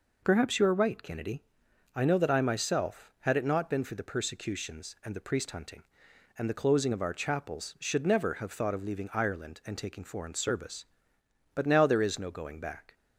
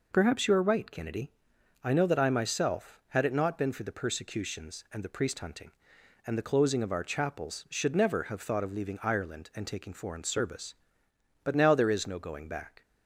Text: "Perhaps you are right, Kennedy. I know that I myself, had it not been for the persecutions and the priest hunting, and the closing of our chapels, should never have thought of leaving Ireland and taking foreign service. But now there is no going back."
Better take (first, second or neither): neither